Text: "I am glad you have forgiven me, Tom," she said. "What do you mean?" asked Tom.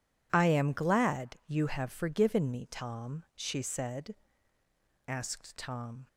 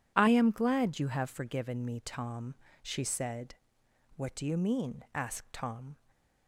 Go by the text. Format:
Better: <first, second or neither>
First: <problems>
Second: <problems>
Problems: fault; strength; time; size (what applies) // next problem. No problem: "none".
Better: second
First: skips "What do you mean"; at 4.6 s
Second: none